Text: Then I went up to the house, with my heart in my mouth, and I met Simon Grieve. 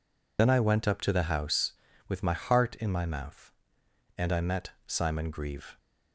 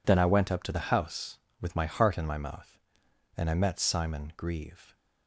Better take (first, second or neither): second